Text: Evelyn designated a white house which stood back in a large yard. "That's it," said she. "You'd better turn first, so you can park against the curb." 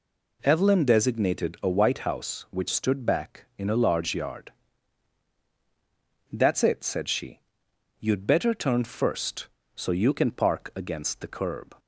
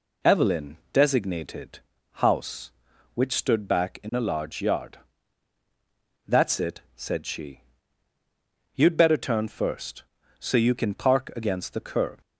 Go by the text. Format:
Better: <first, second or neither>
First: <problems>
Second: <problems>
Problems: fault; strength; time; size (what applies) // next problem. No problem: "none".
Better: first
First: none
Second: skips "a white"; at 1.9 s